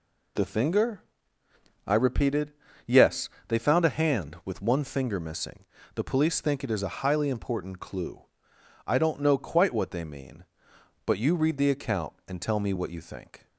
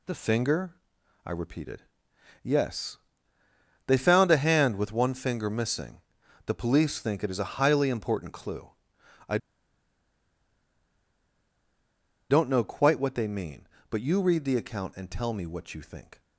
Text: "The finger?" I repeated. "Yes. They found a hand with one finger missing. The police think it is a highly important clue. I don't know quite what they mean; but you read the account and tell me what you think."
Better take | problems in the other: first | pauses between "I" and "don't"; strong; at 9.3 s; 2.9 s long

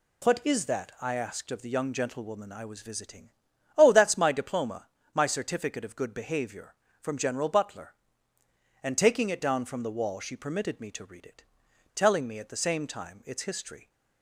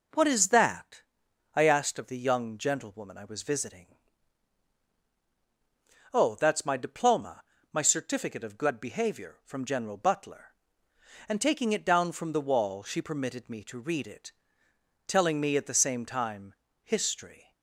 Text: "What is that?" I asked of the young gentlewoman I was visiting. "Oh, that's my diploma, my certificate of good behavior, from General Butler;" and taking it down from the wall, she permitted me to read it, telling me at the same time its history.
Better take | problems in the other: first | skips "its"; at 16.6 s

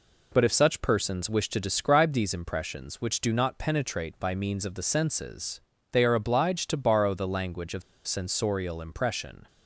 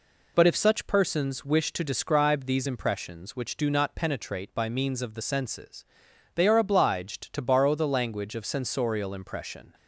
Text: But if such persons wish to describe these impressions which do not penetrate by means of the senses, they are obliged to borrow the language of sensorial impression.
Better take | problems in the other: second | pauses between "of" and "sensorial"; slight; at 7.8 s; 0.25 s long

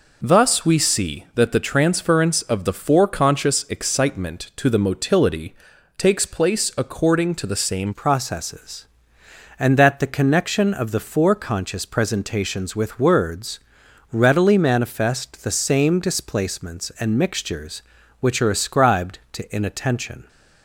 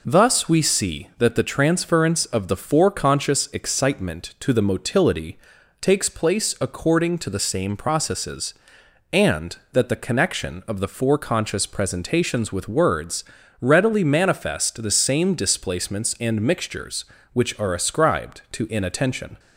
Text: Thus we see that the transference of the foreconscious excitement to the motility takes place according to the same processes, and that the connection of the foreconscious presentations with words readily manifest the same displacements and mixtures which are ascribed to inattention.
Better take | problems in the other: second | pauses between "motility" and "takes"; at 5.5 s; 0.42 s long; also in the second // changes voice at "processes"; from 7.9 s on; 12.3 s long // pauses between "words" and "readily"; noticeable; at 13.5 s; 0.54 s long; slight in the second

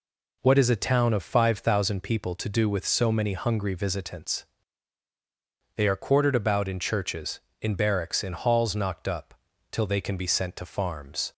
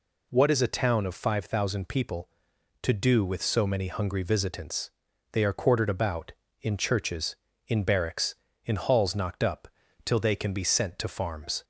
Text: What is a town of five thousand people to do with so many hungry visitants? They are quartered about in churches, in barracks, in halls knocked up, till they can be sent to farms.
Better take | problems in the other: neither | none

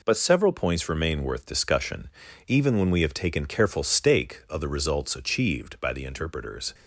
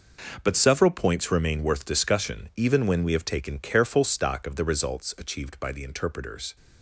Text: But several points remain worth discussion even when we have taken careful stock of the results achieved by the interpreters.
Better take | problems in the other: second | pauses between "discussion" and "even"; at 2.0 s; 0.38 s long // says "stake" for "stock"; at 3.8 s

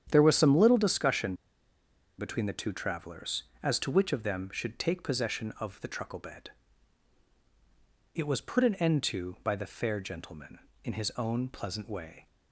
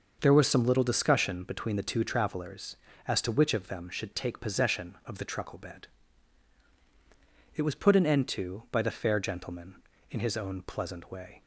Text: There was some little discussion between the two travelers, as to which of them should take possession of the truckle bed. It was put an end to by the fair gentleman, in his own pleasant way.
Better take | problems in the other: second | starts louder than the rest; strong; until 1.1 s; 9 dB; also in the second // pauses between "discussion" and "between"; noticeable; at 1.3 s; 0.84 s long

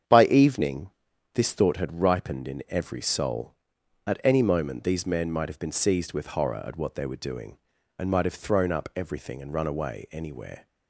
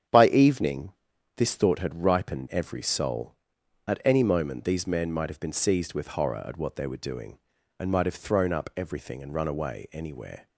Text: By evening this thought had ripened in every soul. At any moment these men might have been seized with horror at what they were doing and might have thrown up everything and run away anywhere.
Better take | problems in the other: first | starts louder than the rest; strong; until 1.5 s; 8 dB; strong in the first // pauses between "evening" and "this"; at 0.9 s; 0.42 s long; also in the first // skips "in"; at 2.4 s

